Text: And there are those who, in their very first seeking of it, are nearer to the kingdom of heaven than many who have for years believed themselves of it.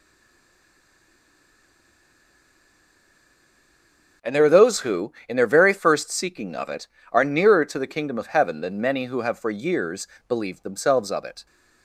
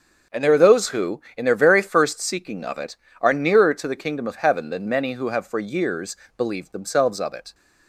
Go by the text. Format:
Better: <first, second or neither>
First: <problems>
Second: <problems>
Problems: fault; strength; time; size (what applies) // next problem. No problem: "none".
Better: second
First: stays silent before the first word; strong; until 4.2 s; 4.2 s long // starts louder than the rest; until 5.3 s; 6.5 dB // pauses between "years" and "believed"; slight; at 10.0 s; 0.20 s long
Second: starts louder than the rest; until 1.4 s; 6.5 dB // pauses between "years" and "believed"; slight; at 6.1 s; 0.20 s long